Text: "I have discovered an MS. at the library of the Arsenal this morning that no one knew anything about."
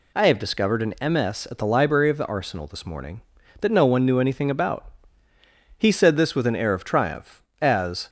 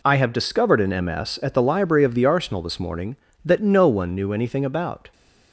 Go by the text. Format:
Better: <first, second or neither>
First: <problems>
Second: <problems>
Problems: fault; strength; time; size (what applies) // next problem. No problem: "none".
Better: second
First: goes on to say "He said this with an air of triumph as"; strong; from 5.7 s on; 2.3 s long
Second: none